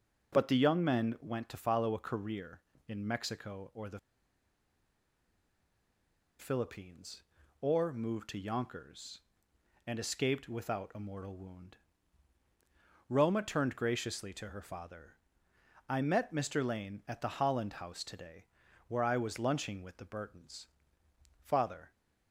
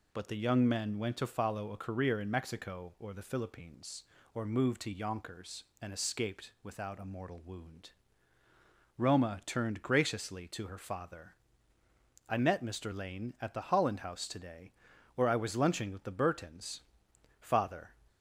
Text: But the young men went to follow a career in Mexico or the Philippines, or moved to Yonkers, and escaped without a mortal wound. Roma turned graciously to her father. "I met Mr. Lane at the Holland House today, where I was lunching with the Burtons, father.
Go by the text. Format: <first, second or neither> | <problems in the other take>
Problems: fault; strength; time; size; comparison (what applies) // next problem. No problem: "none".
second | pauses between "the" and "Philippines"; strong; at 3.9 s; 2.3 s long